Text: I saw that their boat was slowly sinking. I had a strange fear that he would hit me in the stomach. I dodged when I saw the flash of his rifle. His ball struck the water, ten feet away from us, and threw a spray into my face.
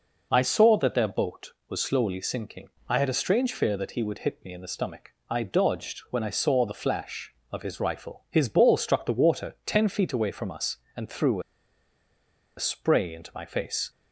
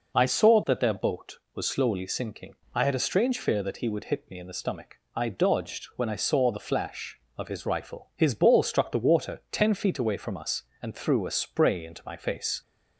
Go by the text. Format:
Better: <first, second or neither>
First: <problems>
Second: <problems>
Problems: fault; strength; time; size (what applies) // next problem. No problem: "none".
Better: second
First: pauses between "threw" and "a"; at 11.3 s; 1.1 s long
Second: none